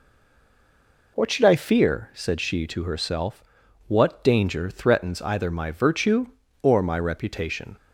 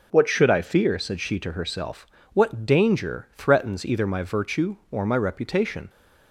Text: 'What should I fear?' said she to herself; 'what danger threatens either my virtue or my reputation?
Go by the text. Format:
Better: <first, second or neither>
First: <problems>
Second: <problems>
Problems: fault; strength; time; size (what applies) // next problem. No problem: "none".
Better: second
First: stays silent before the first word; until 1.1 s; 1.1 s long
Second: none